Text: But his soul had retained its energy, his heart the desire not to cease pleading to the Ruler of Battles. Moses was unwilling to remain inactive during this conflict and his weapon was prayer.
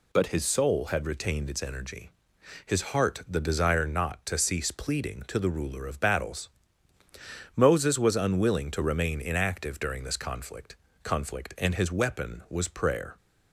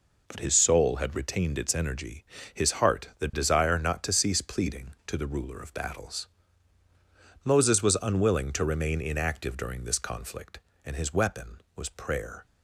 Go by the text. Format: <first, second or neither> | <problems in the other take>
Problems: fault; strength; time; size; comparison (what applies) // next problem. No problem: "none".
second | says "conflict" twice; at 11.0 s